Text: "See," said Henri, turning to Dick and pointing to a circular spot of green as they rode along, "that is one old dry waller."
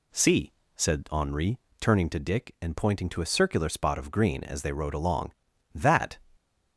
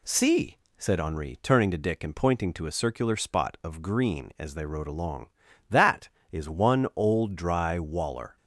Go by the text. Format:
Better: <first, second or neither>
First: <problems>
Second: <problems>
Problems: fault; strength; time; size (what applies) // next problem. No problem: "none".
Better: second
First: stops before "is one old dry waller"; at 6.3 s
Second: none